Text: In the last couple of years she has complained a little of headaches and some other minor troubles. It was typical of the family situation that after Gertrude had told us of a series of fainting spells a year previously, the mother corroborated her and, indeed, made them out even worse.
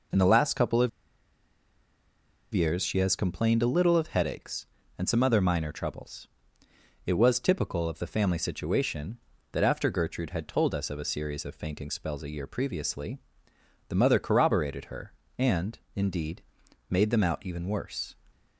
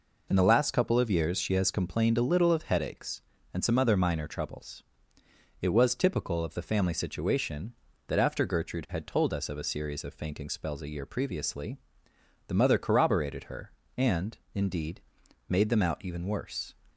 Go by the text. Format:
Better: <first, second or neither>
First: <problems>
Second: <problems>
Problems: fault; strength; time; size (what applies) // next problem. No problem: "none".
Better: second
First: pauses between "of" and "years"; strong; at 0.8 s; 1.6 s long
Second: none